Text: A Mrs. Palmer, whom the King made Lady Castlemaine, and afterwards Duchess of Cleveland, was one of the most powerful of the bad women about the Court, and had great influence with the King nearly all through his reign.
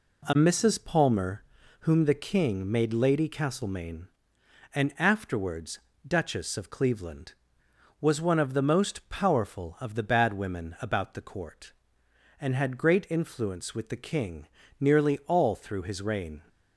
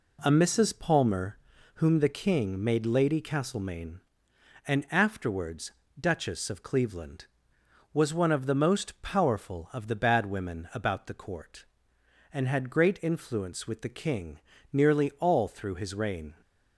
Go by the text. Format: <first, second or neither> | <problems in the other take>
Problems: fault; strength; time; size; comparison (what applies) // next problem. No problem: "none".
neither | pauses between "afterwards" and "Duchess"; slight; the same in both // pauses between "King" and "nearly"; slight; the same in both